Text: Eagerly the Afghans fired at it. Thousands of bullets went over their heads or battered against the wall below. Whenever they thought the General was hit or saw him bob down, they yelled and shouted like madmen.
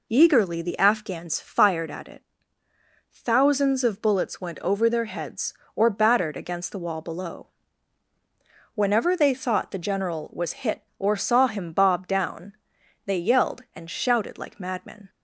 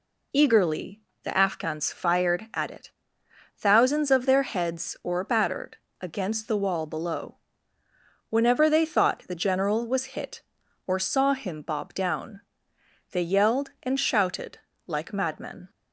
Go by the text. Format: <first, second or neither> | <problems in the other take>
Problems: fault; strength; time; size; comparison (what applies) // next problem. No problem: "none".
first | pauses between "Eagerly" and "the"; slight; at 1.0 s; 0.22 s long // skips "bullets went over"; at 4.2 s // pauses between "battered" and "against"; slight; at 5.7 s; 0.22 s long // pauses between "shouted" and "like"; slight; at 14.5 s; 0.28 s long